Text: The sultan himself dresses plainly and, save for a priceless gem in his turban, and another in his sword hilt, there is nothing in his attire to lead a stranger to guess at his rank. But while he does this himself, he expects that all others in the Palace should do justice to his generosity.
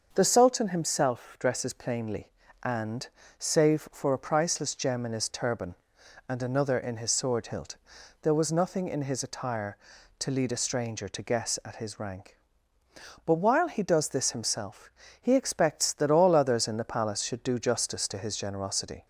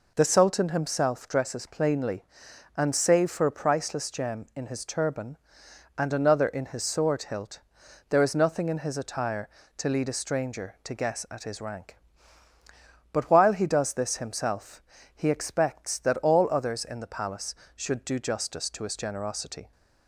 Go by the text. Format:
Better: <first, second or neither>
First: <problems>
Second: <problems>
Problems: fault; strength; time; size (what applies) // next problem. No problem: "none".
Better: second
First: starts louder than the rest; until 1.1 s; 6.5 dB // says "was" for "is"; at 8.3 s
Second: none